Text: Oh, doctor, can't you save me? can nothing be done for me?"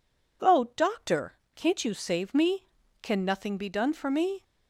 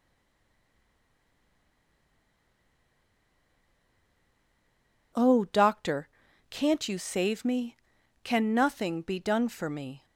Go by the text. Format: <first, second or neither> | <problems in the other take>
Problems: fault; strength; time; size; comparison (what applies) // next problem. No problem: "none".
first | stays silent before the first word; strong; until 5.1 s; 5.1 s long